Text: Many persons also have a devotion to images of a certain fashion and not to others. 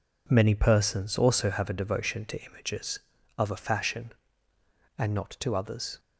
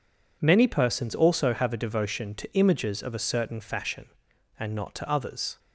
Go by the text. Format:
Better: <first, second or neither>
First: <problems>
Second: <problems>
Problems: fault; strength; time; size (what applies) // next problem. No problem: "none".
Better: second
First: skips "certain"; at 3.5 s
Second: none